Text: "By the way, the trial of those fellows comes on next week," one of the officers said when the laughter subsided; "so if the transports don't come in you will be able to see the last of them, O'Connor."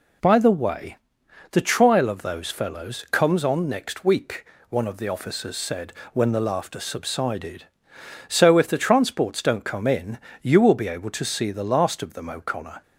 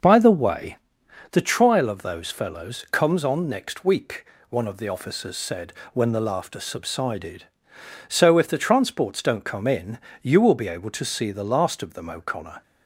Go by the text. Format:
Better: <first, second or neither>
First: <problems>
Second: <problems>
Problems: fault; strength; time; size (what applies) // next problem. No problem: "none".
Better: first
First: pauses between "said" and "when"; slight; at 5.9 s; 0.18 s long // pauses between "in" and "you"; slight; at 10.1 s; 0.24 s long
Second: starts louder than the rest; noticeable; until 1.5 s; 6 dB // pauses between "said" and "when"; slight; at 5.7 s; 0.18 s long // pauses between "in" and "you"; slight; at 9.9 s; 0.24 s long